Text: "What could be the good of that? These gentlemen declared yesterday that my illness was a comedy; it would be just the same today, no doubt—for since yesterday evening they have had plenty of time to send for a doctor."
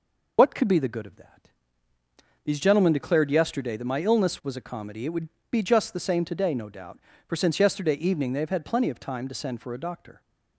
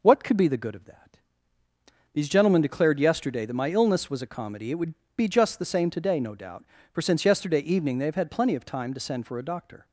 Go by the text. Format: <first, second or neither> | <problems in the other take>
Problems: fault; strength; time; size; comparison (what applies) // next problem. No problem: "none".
second | loses the start of "What"; at 0.3 s; 55 ms // pauses between "would" and "be"; slight; at 5.2 s; 0.22 s long; slight in the second